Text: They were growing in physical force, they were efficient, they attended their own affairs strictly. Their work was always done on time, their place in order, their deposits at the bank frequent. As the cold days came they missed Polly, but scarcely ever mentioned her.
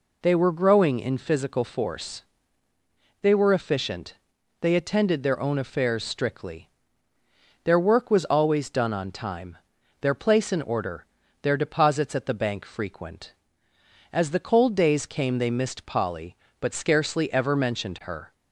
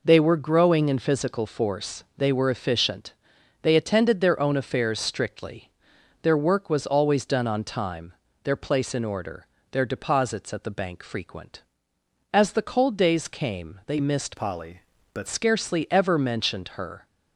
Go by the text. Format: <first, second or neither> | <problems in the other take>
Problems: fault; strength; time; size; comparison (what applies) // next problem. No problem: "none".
first | changes voice from "Polly" to "but"; from 14.3 to 15.2 s; 0.9 s long